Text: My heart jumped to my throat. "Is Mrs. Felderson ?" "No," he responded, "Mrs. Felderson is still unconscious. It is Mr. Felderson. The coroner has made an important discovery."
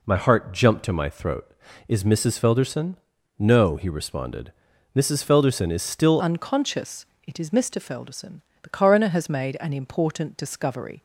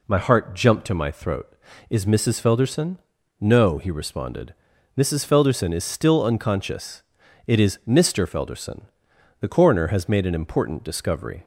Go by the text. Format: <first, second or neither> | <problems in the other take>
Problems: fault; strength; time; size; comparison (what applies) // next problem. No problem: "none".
second | changes voice at "unconscious"; from 6.2 s on; 4.8 s long